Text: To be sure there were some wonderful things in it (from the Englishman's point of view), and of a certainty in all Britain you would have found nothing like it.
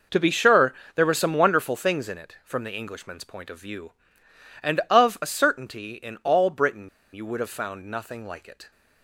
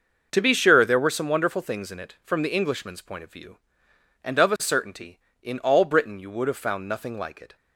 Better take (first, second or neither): second